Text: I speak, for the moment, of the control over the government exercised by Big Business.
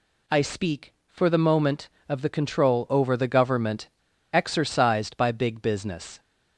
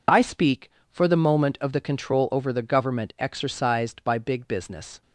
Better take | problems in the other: second | pauses between "government" and "exercised"; at 3.8 s; 0.45 s long

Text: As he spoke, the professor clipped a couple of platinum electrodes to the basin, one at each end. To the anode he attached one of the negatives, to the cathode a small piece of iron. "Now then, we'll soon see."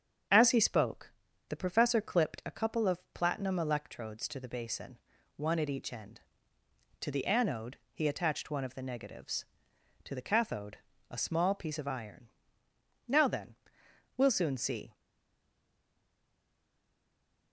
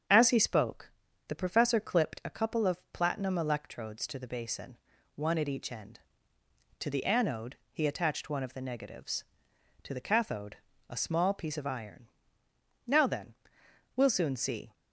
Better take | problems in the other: second | starts louder than the rest; strong; until 1.6 s; 7.5 dB; strong in the second // pauses between "anode" and "he"; slight; at 7.7 s; 0.16 s long; slight in the second // pauses between "cathode" and "a"; slight; at 10.7 s; 0.32 s long; slight in the second // stays silent after the last word; strong; from 14.9 s on; 2.6 s long

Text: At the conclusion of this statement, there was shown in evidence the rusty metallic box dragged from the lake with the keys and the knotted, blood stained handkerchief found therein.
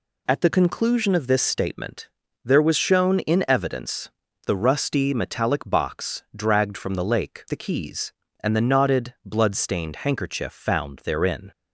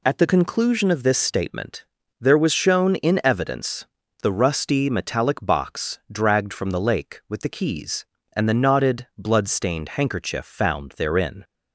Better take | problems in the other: second | pauses between "evidence" and "the"; at 4.0 s; 0.38 s long; also in the second // skips "with"; at 7.4 s

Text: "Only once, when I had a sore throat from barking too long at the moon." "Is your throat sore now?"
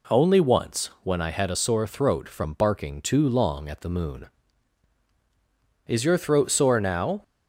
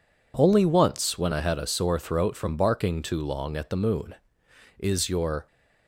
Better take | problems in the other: first | stops before "throat sore now"; at 5.4 s

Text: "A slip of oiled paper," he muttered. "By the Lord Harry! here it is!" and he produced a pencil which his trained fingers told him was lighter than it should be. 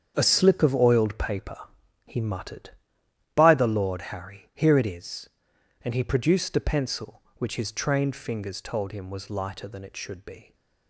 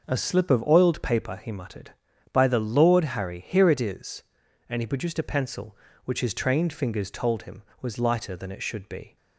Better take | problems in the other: second | gets quieter; strong; throughout; 12 dB // starts louder than the rest; strong; until 1.1 s; 7.5 dB; also in the second

